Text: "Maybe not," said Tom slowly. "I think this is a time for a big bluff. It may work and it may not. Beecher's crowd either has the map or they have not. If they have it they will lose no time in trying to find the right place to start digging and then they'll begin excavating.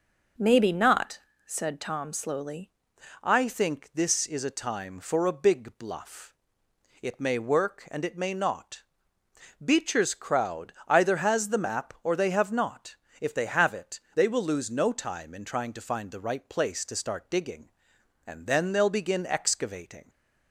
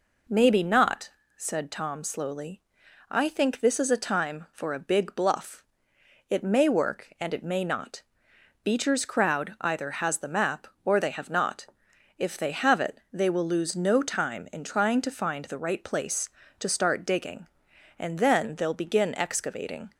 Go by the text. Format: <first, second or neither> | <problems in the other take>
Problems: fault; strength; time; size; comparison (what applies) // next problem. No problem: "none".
second | changes voice at "I"; from 3.2 s on; 16.8 s long // pauses between "it" and "they"; slight; at 13.9 s; 0.16 s long